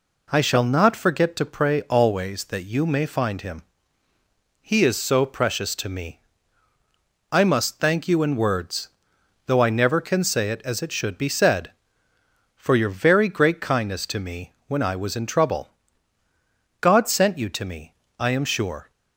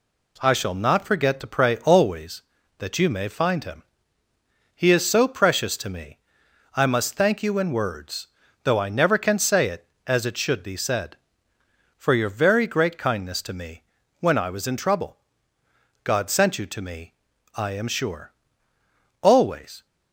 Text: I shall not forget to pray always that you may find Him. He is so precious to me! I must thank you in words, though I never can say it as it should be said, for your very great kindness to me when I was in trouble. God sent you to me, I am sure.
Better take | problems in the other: first | pauses between "me" and "when"; slight; at 13.8 s; 0.36 s long; slight in the first // goes on to say "Always"; noticeable; from 19.2 s on; 0.64 s long

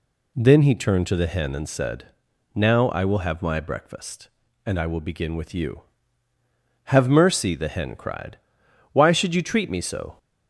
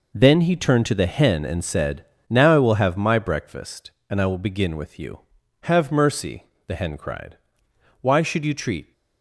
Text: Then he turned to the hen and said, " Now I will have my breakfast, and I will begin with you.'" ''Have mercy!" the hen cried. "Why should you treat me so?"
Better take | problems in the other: first | stops before "me so"; at 8.9 s

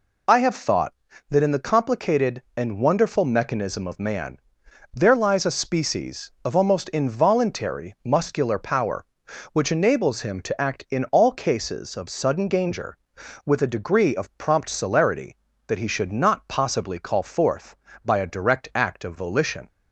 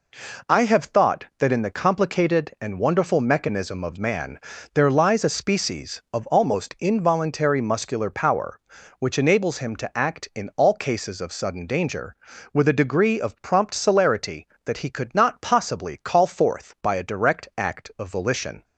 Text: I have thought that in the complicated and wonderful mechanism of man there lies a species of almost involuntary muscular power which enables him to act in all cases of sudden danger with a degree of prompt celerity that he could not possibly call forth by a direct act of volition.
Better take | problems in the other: second | pauses between "man" and "there"; noticeable; at 4.3 s; 0.56 s long; slight in the second // says "should" for "could"; at 15.8 s

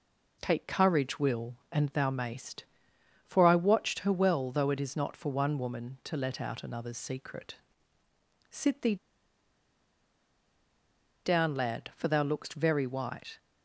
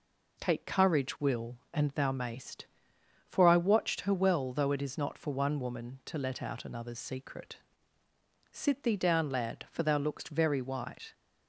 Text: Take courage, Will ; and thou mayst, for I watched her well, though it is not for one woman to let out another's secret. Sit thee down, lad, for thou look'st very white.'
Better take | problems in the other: second | pauses between "thee" and "down"; strong; at 8.9 s; 2.2 s long

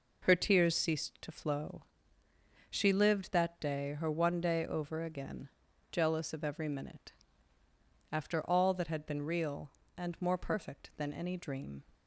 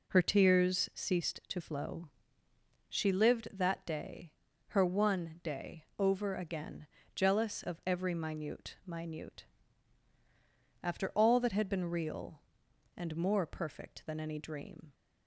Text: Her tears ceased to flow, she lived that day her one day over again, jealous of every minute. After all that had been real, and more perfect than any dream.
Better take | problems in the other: first | pauses between "day" and "her"; slight; at 4.3 s; 0.36 s long // says "minute" twice; at 8.8 s

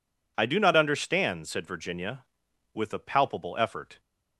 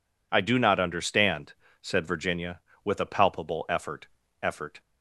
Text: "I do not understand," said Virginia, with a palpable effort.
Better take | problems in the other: first | says "effort" twice; at 4.4 s

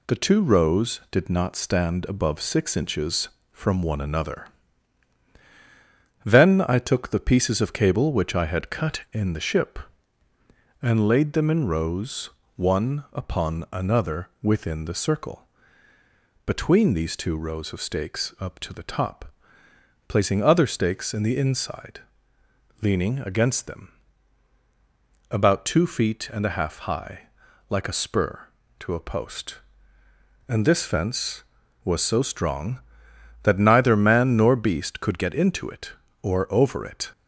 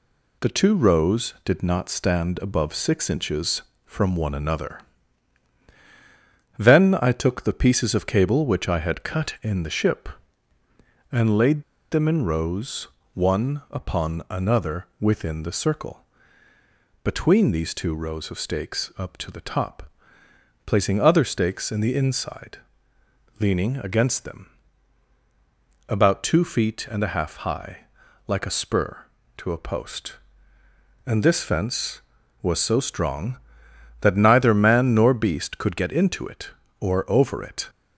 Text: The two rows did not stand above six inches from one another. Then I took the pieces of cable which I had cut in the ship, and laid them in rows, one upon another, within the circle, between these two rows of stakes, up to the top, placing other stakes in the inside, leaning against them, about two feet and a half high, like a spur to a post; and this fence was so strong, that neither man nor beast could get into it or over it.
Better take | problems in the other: first | pauses between "laid" and "them"; slight; at 11.6 s; 0.29 s long

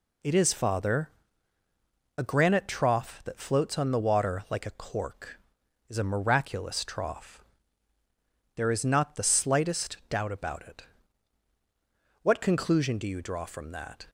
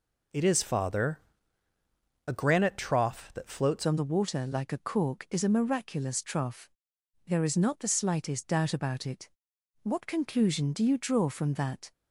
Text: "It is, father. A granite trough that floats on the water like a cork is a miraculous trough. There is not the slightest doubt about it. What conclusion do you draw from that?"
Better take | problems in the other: first | changes voice at "on"; from 3.8 s on; 8.1 s long

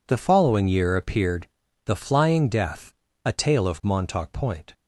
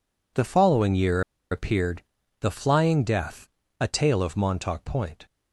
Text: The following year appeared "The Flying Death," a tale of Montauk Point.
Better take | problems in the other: first | pauses between "year" and "appeared"; slight; at 1.2 s; 0.30 s long // pauses between "appeared" and "The"; at 2.0 s; 0.38 s long; also in the first

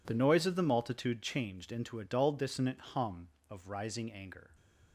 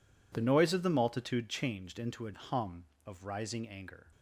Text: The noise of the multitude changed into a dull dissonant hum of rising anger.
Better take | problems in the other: first | skips "dull dissonant"; at 2.3 s

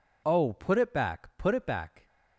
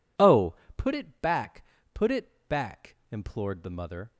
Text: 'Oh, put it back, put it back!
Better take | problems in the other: first | goes on to say "implored the mother"; noticeable; from 3.1 s on; 1.0 s long

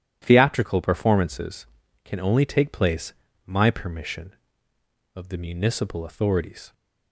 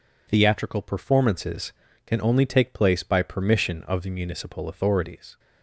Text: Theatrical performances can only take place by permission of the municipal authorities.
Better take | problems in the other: second | says "my" for "by"; at 3.4 s

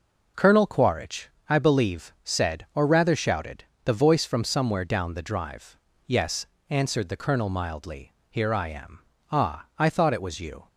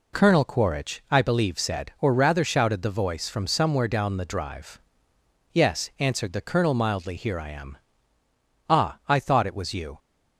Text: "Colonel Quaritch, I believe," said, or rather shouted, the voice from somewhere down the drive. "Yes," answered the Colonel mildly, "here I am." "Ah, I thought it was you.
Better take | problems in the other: neither | none

